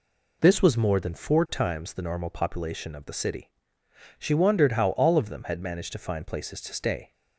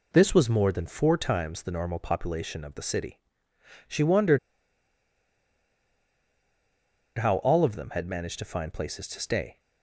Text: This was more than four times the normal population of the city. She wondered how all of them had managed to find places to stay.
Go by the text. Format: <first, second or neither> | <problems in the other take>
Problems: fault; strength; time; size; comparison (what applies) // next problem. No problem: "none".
first | pauses between "wondered" and "how"; strong; at 4.3 s; 2.7 s long